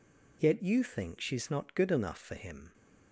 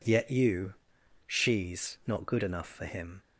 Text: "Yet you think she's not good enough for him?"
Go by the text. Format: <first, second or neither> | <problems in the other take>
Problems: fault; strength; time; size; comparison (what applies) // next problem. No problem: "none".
first | skips "think"; at 1.0 s